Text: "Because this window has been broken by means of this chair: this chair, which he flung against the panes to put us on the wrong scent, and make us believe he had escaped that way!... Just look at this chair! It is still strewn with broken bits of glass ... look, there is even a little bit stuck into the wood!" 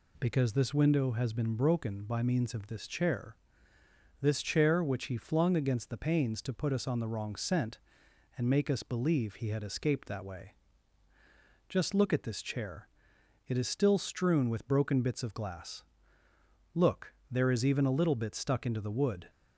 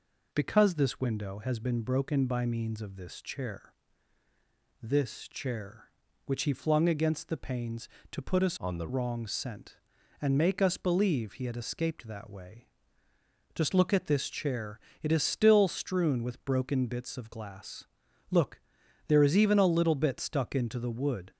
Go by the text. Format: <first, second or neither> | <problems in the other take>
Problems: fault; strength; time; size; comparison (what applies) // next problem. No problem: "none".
first | changes voice from "on" to "the"; from 8.5 to 8.8 s; 0.3 s long